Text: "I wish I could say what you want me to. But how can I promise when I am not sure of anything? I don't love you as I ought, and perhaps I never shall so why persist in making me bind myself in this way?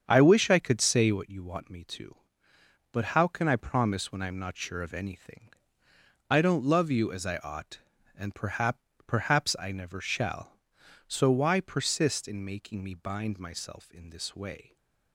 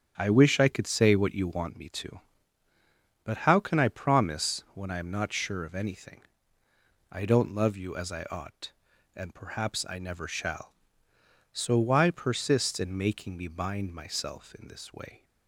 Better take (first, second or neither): second